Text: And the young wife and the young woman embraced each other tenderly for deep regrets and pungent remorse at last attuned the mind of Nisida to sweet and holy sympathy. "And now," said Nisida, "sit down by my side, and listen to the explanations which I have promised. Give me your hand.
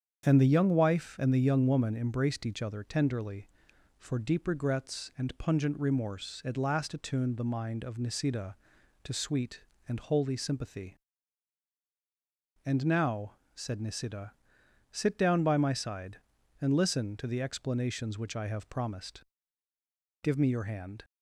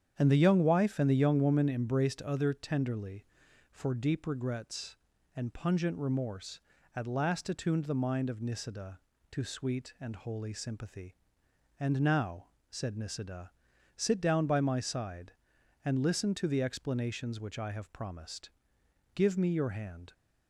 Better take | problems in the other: first | starts louder than the rest; strong; until 1.1 s; 8.5 dB; strong in the first // skips "each"; at 2.2 s

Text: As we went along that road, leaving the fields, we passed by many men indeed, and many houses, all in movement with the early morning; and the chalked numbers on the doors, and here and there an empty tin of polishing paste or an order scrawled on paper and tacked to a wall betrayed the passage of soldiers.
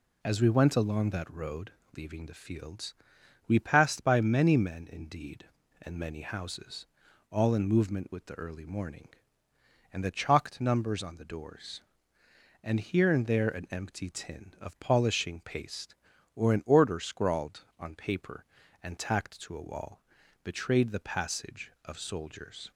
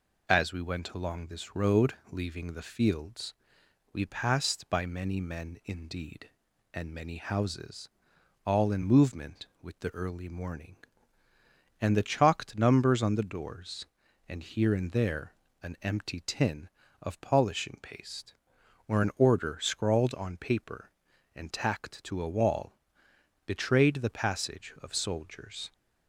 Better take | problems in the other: first | says "this" for "that"; at 1.2 s // pauses between "there" and "an"; slight; at 15.3 s; 0.28 s long // pauses between "wall" and "betrayed"; noticeable; at 22.7 s; 0.68 s long; also in the first

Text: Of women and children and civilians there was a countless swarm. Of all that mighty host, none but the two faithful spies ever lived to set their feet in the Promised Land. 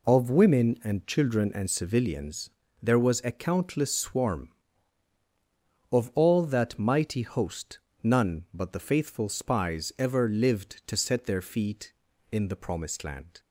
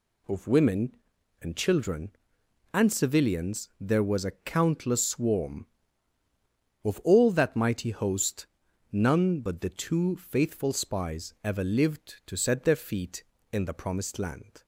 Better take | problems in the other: second | pauses between "civilians" and "there"; slight; at 2.4 s; 0.32 s long // skips "two"; at 8.7 s

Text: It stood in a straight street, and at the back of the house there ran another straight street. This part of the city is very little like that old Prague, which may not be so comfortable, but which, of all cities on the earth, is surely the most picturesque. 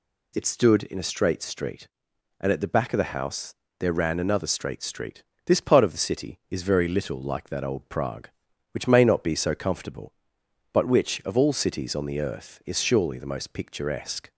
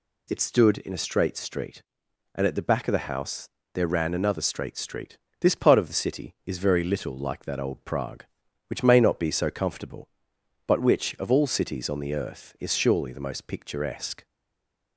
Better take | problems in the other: first | pauses between "house" and "there"; slight; at 3.4 s; 0.24 s long; slight in the first // stays silent after the last word; slight; from 14.2 s on; 0.7 s long

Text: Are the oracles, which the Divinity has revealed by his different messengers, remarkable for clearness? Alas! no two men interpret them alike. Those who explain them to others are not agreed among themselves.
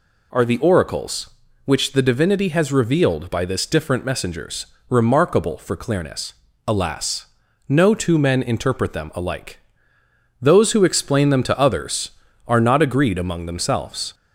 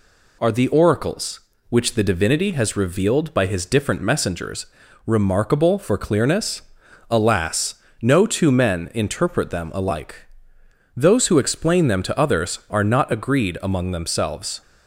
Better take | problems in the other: second | says "this" for "his"; at 3.4 s

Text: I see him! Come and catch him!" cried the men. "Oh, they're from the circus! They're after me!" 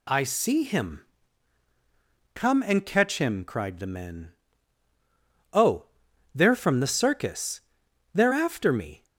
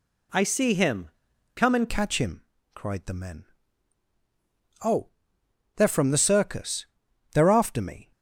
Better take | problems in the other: first | changes voice at "catch"; from 1.8 s on; 6.3 s long

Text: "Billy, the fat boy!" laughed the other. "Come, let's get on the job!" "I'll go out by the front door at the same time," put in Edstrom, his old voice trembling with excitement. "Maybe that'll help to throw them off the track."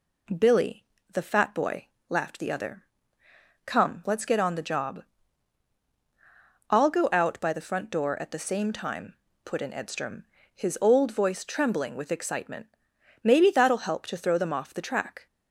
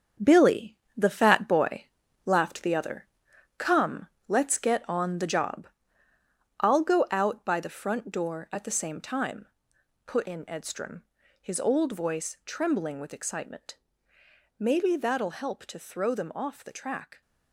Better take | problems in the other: first | gets quieter; strong; throughout; 8 dB

